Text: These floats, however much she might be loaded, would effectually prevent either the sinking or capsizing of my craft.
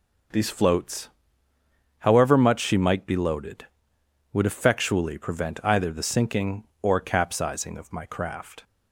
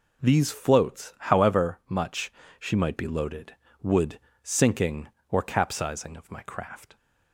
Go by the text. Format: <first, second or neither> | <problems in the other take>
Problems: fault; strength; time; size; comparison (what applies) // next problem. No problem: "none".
first | pauses between "much" and "she"; slight; at 2.2 s; 0.30 s long // skips "effectually prevent either the"; at 4.3 s